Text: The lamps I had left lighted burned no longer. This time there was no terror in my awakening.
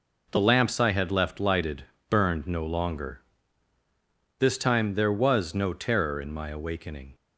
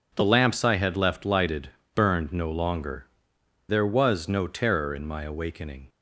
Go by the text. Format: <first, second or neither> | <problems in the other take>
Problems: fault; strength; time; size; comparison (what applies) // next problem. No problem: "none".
first | pauses between "lighted" and "burned"; slight; at 1.7 s; 0.24 s long; slight in the first // skips "This time"; at 3.3 s